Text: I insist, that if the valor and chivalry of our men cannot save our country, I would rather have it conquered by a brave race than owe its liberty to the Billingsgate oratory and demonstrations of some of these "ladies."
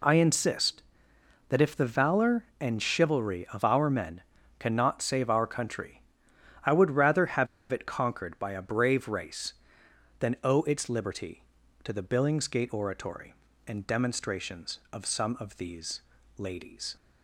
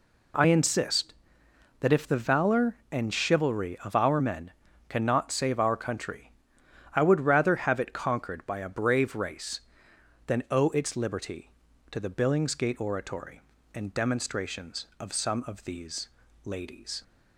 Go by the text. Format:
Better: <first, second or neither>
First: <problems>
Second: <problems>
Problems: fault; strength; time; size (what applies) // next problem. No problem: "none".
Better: second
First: pauses between "men" and "cannot"; at 4.2 s; 0.38 s long // pauses between "have" and "it"; slight; at 7.4 s; 0.24 s long // pauses between "these" and "ladies"; slight; at 16.0 s; 0.36 s long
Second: pauses between "men" and "cannot"; at 4.5 s; 0.38 s long // pauses between "these" and "ladies"; slight; at 16.0 s; 0.36 s long